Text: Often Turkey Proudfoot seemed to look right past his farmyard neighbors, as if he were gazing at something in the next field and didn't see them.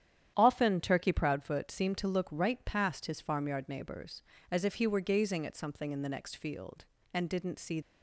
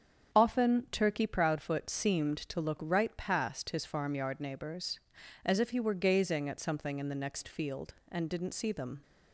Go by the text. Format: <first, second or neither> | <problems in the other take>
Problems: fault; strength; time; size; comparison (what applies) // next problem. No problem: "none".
second | starts louder than the rest; strong; until 1.3 s; 10 dB; strong in the second // stops before "them"; at 7.8 s